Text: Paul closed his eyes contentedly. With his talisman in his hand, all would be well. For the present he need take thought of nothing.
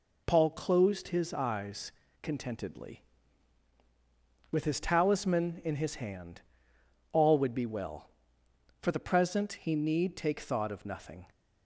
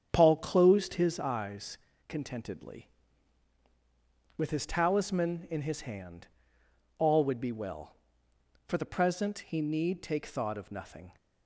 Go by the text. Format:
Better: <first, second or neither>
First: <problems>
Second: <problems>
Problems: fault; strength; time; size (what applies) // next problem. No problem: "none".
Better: first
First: pauses between "eyes" and "contentedly"; slight; at 1.9 s; 0.30 s long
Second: starts louder than the rest; strong; until 1.4 s; 8.5 dB // pauses between "eyes" and "contentedly"; slight; at 1.7 s; 0.30 s long